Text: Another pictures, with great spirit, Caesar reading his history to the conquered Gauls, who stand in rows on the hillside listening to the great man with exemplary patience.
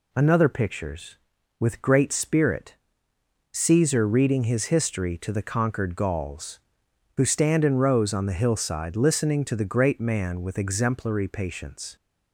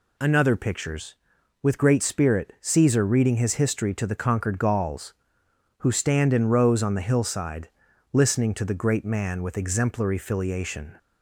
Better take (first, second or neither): first